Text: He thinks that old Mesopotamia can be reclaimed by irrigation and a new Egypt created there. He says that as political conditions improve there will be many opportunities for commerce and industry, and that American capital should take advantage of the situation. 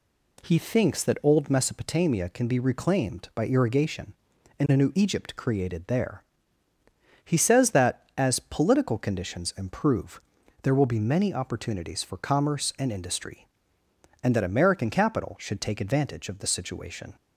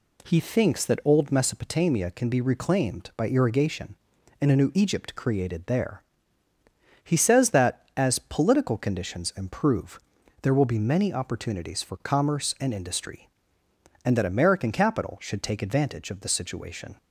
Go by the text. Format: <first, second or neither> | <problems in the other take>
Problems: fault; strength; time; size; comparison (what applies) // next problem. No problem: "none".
neither | pauses between "improve" and "there"; the same in both